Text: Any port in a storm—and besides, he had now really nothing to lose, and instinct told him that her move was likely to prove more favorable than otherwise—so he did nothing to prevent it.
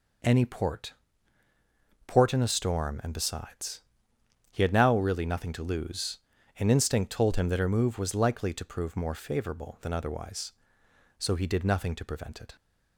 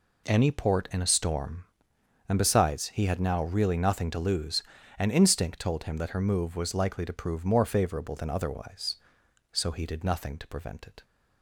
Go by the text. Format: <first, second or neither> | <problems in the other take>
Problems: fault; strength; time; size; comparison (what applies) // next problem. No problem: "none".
second | says "port" twice; at 2.0 s